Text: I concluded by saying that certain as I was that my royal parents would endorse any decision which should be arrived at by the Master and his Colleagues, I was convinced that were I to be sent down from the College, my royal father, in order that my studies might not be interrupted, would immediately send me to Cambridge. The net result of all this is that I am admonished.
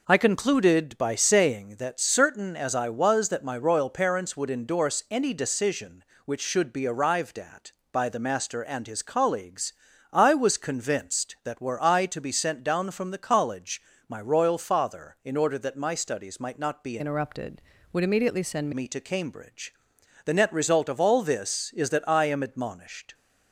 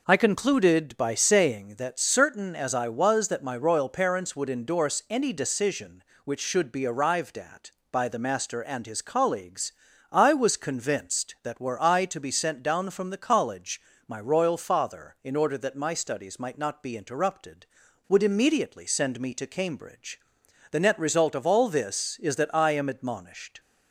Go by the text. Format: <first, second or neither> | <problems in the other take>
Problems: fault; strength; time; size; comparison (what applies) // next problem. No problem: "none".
second | changes voice from "interrupted" to "send"; from 16.9 to 18.7 s; 1.8 s long